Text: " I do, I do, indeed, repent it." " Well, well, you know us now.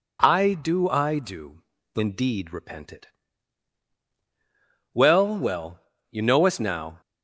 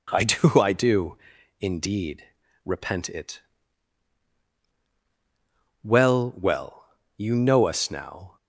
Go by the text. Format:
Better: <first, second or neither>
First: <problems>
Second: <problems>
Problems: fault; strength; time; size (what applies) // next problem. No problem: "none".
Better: neither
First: none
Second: none